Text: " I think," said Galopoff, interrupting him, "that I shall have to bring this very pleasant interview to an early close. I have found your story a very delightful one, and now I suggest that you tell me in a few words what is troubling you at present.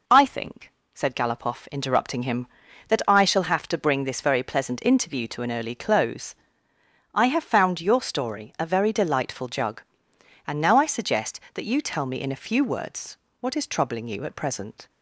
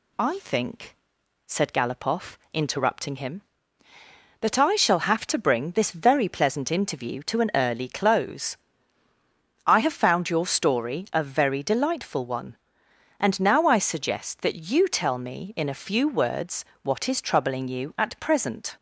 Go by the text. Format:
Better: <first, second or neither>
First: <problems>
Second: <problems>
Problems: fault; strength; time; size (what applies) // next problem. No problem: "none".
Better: second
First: says "jug" for "one"; at 9.4 s // pauses between "words" and "what"; slight; at 13.1 s; 0.24 s long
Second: pauses between "words" and "what"; slight; at 16.6 s; 0.18 s long